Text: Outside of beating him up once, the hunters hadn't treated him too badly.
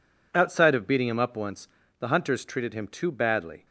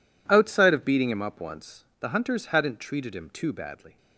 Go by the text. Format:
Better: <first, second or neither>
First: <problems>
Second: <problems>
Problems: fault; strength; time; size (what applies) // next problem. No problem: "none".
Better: second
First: skips "hadn't"; at 2.4 s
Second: none